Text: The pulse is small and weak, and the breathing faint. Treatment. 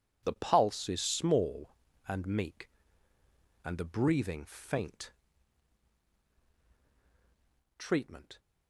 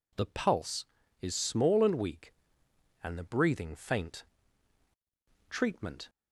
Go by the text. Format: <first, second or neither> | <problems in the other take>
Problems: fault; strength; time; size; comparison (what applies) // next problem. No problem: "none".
second | says "meek" for "weak"; at 2.2 s